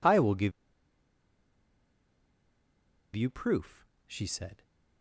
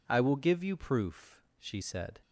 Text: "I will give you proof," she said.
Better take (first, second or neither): second